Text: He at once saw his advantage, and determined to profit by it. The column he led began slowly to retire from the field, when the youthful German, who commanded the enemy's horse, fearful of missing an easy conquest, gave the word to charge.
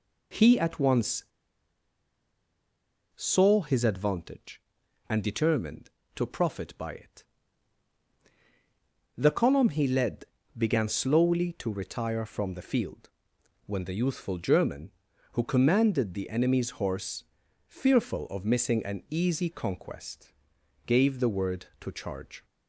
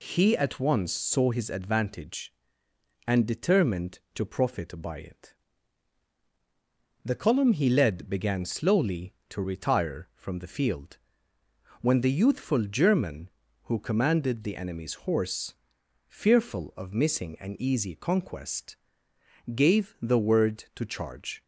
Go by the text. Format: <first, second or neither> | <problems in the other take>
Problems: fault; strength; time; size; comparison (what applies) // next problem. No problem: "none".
second | pauses between "once" and "saw"; strong; at 1.2 s; 1.9 s long // pauses between "led" and "began"; slight; at 10.2 s; 0.30 s long